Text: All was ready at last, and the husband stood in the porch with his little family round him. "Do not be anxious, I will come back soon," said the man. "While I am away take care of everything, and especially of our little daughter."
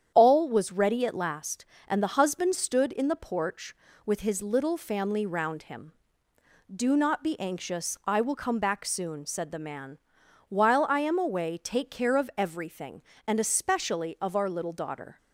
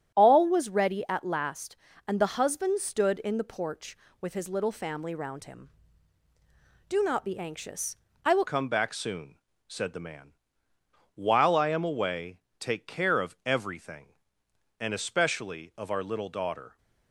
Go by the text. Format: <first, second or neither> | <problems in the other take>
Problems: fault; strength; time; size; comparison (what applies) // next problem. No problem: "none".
first | starts louder than the rest; strong; until 1.1 s; 9.5 dB; strong in the first // changes voice at "come"; from 8.4 s on; 8.3 s long // pauses between "away" and "take"; slight; at 12.3 s; 0.22 s long